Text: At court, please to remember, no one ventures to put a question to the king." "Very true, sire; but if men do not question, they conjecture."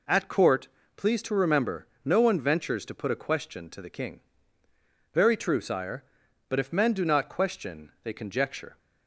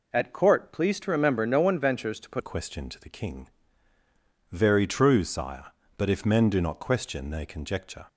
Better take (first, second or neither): first